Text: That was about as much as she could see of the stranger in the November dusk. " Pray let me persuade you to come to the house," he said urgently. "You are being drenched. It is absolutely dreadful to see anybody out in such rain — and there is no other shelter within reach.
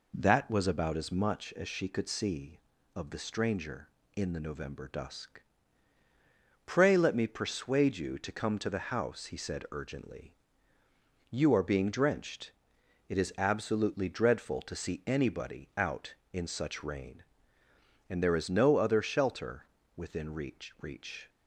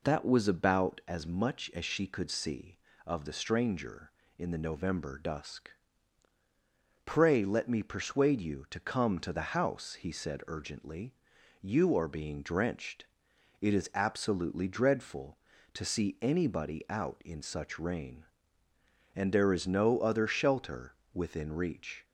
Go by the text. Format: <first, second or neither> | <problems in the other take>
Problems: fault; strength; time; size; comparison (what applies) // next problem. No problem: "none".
second | pauses between "shelter" and "within"; slight; at 19.6 s; 0.32 s long; slight in the second // says "reach" twice; at 20.8 s